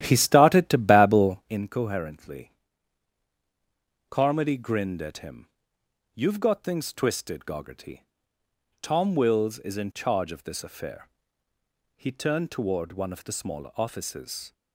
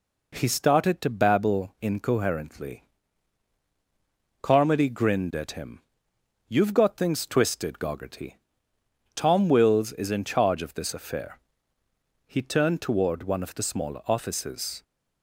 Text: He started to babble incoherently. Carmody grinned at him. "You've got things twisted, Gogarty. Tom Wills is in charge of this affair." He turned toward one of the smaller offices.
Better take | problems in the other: second | starts louder than the rest; strong; until 1.6 s; 12 dB

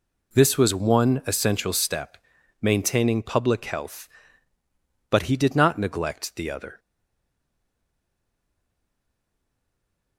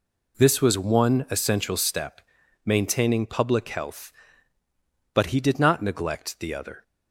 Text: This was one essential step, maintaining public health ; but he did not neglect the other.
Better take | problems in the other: second | stays silent after the last word; strong; from 6.7 s on; 3.4 s long

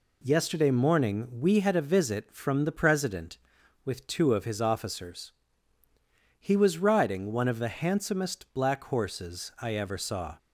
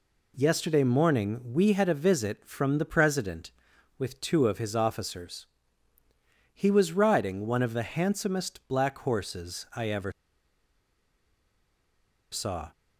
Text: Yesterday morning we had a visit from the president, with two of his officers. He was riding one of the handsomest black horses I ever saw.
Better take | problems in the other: first | pauses between "ever" and "saw"; strong; at 10.1 s; 2.2 s long

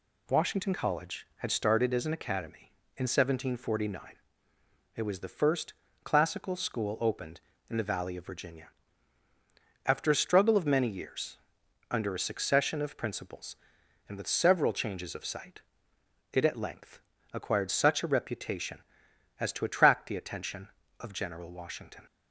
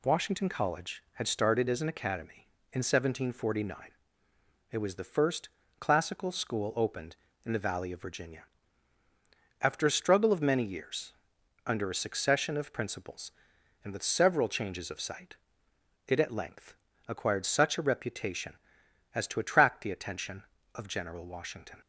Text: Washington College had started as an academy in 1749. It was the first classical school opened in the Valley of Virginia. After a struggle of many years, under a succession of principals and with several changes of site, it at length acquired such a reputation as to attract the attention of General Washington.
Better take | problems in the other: neither | pauses between "first" and "classical"; slight; the same in both // pauses between "length" and "acquired"; slight; the same in both

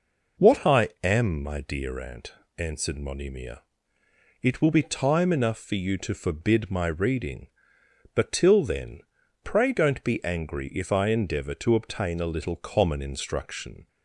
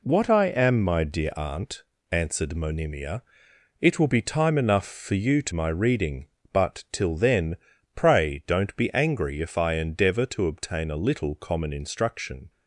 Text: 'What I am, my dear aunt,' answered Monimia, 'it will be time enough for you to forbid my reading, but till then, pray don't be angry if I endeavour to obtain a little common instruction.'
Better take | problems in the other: first | skips "forbid"; at 5.5 s

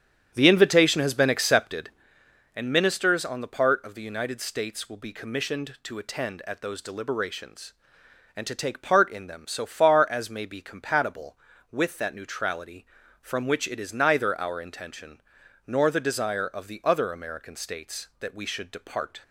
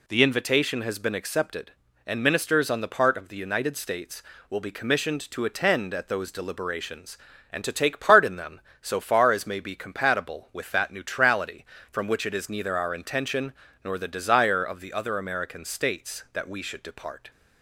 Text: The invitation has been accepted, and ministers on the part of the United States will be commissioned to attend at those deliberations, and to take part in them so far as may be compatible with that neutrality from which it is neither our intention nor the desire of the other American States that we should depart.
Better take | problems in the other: second | starts louder than the rest; strong; until 2.1 s; 9.5 dB // pauses between "intention" and "nor"; noticeable; at 15.2 s; 0.46 s long; slight in the second

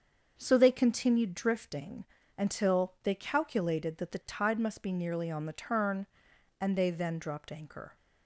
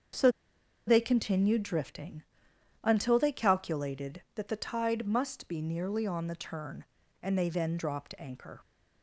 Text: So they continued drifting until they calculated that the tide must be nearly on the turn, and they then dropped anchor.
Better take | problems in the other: first | starts louder than the rest; until 1.7 s; 7 dB; also in the first // pauses between "So" and "they"; noticeable; at 0.3 s; 0.56 s long // pauses between "drifting" and "until"; noticeable; at 2.2 s; 0.62 s long; slight in the first

